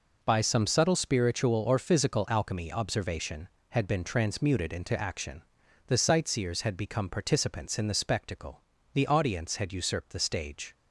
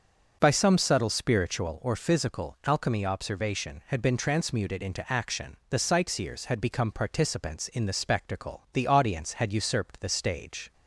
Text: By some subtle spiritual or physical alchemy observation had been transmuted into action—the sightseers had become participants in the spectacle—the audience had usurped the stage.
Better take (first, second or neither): first